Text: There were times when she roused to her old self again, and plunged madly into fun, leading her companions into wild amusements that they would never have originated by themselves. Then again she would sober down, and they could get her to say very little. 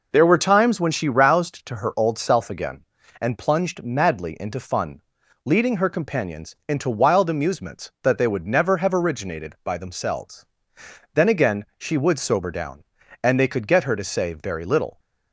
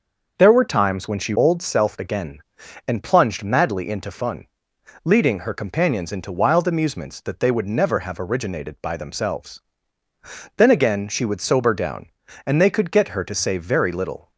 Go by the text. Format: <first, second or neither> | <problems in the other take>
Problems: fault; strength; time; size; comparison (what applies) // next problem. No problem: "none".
first | starts louder than the rest; until 1.4 s; 6 dB // skips "roused to her"; at 1.3 s